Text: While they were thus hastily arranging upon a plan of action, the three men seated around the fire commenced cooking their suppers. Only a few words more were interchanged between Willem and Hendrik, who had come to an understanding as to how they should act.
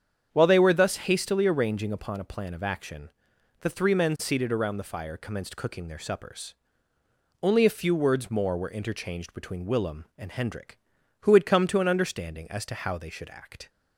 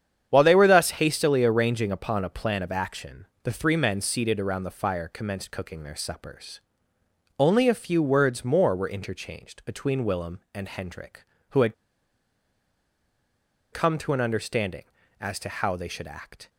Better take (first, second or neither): first